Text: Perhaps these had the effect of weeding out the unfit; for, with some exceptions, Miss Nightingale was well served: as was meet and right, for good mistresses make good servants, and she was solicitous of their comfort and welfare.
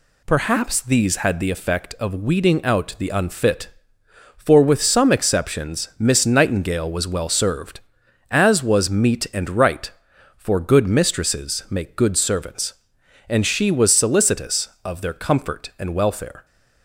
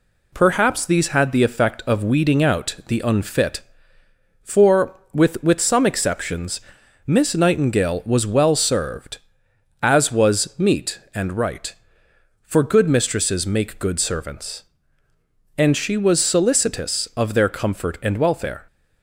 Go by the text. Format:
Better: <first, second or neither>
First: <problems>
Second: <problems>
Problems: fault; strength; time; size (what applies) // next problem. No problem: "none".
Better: first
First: none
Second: says "with" twice; at 5.4 s